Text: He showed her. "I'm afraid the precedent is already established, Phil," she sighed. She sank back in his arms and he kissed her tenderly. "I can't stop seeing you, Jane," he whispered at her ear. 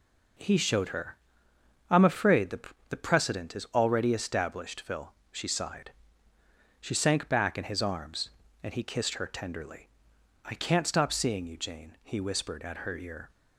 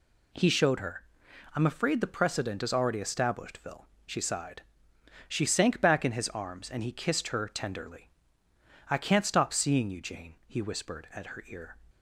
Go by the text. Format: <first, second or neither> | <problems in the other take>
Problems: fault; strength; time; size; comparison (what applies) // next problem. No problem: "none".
second | says "the" twice; at 2.8 s